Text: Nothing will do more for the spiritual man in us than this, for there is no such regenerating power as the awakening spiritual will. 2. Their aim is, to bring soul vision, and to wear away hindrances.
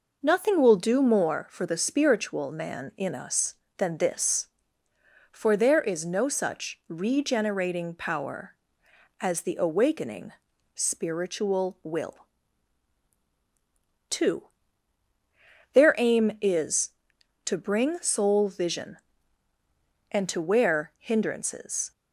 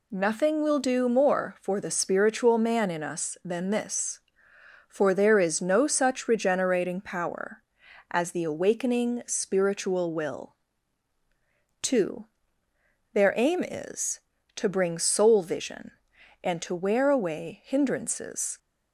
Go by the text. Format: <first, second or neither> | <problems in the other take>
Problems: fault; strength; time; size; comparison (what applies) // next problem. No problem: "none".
second | pauses between "awakening" and "spiritual"; at 10.3 s; 0.42 s long // skips "away"; at 20.9 s